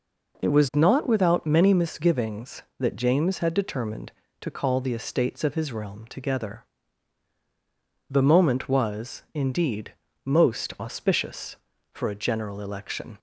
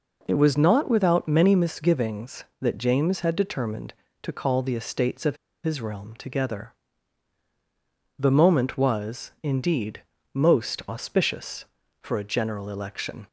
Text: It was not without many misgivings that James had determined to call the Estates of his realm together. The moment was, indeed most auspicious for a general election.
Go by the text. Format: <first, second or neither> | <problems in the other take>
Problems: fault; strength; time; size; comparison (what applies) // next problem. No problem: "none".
first | pauses between "of" and "his"; slight; at 5.3 s; 0.27 s long // pauses between "indeed" and "most"; slight; at 10.0 s; 0.30 s long; slight in the first